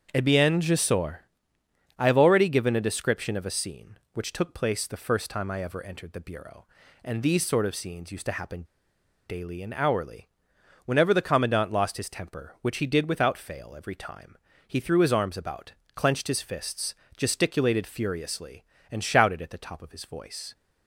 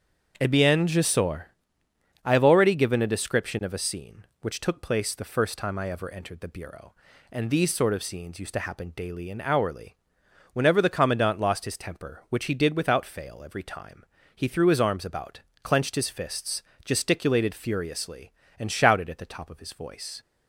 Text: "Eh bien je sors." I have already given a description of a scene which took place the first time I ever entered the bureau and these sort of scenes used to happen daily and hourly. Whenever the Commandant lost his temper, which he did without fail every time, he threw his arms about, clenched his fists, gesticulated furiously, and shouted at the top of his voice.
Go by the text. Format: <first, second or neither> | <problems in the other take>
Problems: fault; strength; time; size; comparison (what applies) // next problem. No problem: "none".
second | starts louder than the rest; until 1.1 s; 7 dB; also in the second // pauses between "happen" and "daily"; noticeable; at 8.6 s; 0.62 s long